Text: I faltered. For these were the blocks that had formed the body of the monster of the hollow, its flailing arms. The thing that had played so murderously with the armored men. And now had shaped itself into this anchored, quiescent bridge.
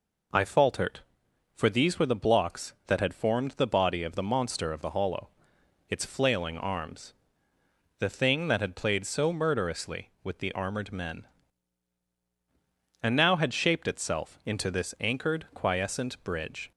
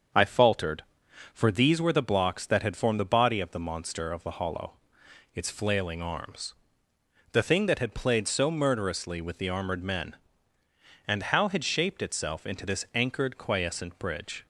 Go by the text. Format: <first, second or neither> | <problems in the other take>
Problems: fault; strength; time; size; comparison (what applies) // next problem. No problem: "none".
first | starts louder than the rest; until 1.6 s; 7 dB // says "how" for "now"; at 11.2 s